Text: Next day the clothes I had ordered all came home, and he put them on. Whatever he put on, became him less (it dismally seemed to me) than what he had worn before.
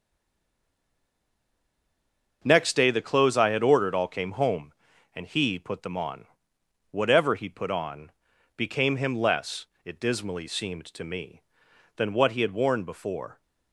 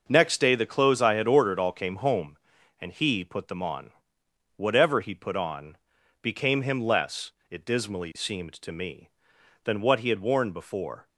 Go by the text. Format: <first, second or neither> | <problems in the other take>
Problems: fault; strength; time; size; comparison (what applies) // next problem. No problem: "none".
second | stays silent before the first word; until 2.4 s; 2.4 s long // starts louder than the rest; noticeable; until 3.4 s; 6 dB; noticeable in the second